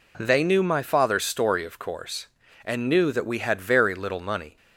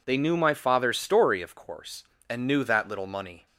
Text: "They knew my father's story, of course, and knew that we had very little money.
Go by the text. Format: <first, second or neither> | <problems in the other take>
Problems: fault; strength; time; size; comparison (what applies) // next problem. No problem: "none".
first | skips "we had very"; at 2.8 s